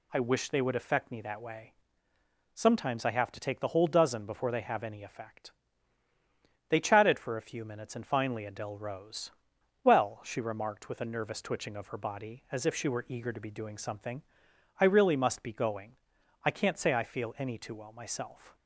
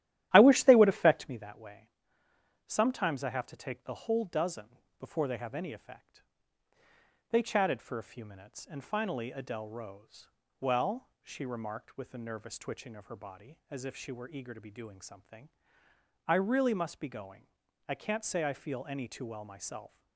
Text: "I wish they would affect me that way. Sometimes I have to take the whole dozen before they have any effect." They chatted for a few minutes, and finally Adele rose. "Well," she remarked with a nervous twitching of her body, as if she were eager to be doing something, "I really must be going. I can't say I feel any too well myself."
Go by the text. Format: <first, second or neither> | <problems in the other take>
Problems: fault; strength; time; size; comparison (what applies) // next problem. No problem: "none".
first | starts louder than the rest; strong; until 1.4 s; 13.5 dB // pauses between "dozen" and "before"; slight; at 4.7 s; 0.21 s long